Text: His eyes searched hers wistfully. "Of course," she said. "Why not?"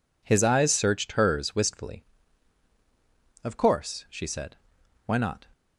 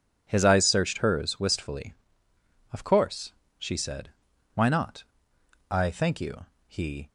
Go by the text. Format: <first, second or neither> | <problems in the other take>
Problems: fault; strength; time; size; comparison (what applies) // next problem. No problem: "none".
first | goes on to say "I thank you he"; from 5.6 s on; 1.3 s long